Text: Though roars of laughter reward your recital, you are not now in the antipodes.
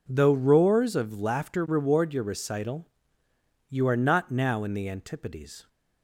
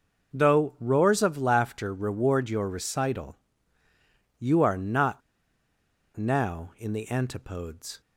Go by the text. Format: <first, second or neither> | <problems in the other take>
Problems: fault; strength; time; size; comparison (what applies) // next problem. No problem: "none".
first | pauses between "not" and "now"; noticeable; at 5.2 s; 0.95 s long